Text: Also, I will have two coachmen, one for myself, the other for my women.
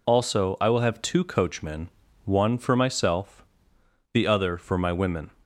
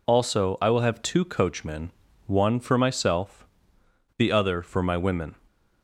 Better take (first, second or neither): neither